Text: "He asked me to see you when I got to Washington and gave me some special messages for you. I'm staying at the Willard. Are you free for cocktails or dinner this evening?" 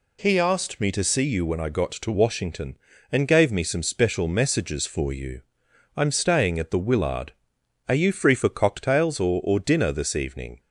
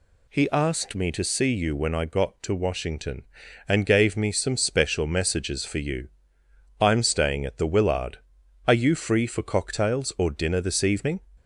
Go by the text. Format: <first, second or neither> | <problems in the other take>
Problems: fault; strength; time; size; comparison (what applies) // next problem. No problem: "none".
second | says "or" twice; at 9.4 s